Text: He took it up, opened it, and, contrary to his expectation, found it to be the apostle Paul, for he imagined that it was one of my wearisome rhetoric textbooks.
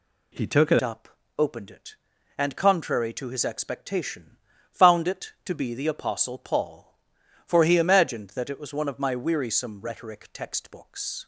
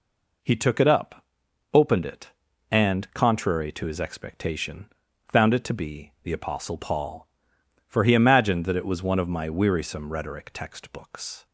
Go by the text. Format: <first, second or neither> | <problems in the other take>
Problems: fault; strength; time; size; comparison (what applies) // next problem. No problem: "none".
second | changes voice at "up"; from 0.8 s on; 10.4 s long